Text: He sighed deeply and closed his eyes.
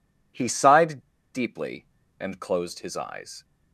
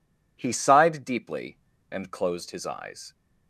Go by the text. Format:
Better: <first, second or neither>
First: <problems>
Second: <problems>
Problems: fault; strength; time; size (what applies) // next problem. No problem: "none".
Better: second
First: pauses between "sighed" and "deeply"; slight; at 0.9 s; 0.34 s long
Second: none